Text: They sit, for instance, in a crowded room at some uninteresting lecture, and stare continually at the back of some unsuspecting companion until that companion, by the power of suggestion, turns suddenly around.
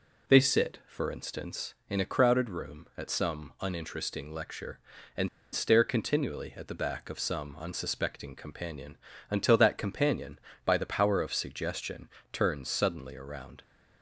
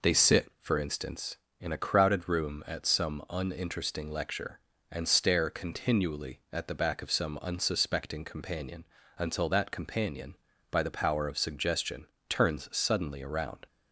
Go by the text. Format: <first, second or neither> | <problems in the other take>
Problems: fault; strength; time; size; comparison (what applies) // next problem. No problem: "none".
second | pauses between "and" and "stare"; slight; at 5.2 s; 0.25 s long // pauses between "companion" and "until"; slight; at 8.9 s; 0.32 s long; slight in the second